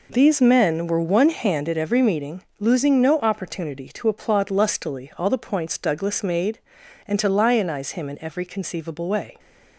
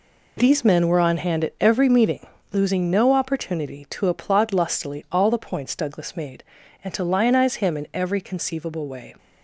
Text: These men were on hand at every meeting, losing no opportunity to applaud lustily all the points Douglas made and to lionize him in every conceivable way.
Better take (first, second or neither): second